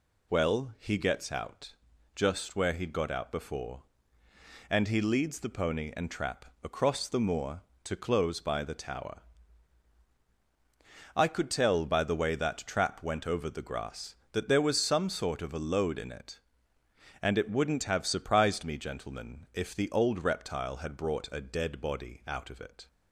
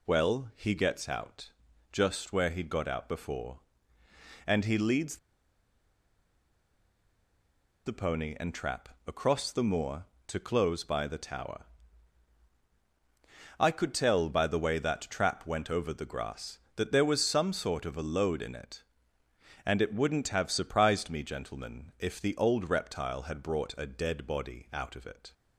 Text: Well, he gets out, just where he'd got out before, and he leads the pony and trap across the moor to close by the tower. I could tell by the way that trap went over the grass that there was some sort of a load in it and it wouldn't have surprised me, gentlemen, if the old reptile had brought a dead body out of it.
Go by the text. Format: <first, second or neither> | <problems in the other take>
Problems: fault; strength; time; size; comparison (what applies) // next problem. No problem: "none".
first | pauses between "leads" and "the"; strong; at 5.1 s; 2.6 s long // pauses between "trap" and "across"; slight; at 8.8 s; 0.16 s long; slight in the first